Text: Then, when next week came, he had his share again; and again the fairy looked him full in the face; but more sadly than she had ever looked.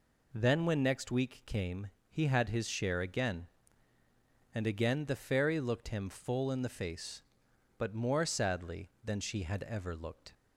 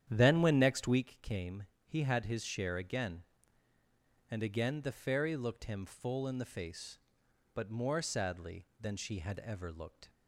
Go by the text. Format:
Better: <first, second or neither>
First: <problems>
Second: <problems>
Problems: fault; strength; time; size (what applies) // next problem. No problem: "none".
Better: first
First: none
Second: starts louder than the rest; strong; until 1.1 s; 10 dB